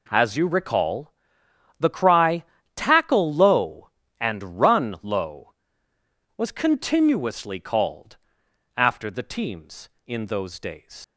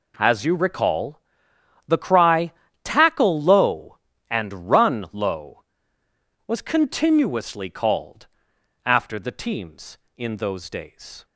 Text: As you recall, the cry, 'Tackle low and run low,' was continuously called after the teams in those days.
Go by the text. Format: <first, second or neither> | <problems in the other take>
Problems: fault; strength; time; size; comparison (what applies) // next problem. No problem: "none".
second | pauses between "called" and "after"; noticeable; at 8.1 s; 0.60 s long; noticeable in the second // leaves "days" unfinished; at 11.0 s; 110 ms